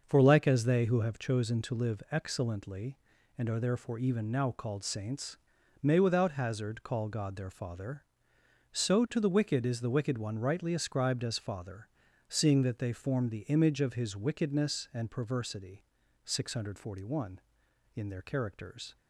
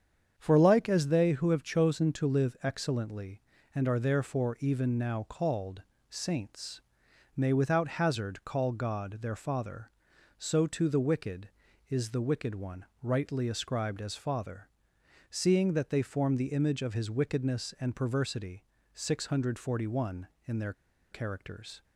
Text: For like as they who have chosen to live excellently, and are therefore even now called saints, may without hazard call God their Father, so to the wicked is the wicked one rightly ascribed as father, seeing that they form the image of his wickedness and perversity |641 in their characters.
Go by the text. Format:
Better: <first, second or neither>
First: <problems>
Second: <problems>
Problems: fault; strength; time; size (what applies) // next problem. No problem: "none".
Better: first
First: starts louder than the rest; noticeable; until 1.0 s; 6 dB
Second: starts louder than the rest; strong; until 1.3 s; 7.5 dB // pauses between "called" and "saints"; slight; at 5.8 s; 0.26 s long // pauses between "one" and "rightly"; slight; at 12.8 s; 0.18 s long // pauses between "their" and "characters"; at 20.7 s; 0.38 s long